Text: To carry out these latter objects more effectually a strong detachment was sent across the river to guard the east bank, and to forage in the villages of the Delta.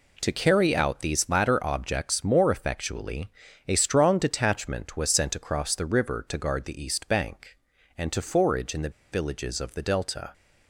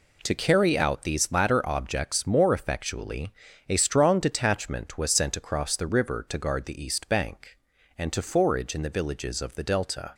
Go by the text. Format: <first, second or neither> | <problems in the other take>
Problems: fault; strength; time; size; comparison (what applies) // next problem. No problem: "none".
second | pauses between "effectually" and "a"; at 3.2 s; 0.38 s long; also in the second // pauses between "the" and "villages"; slight; at 8.8 s; 0.22 s long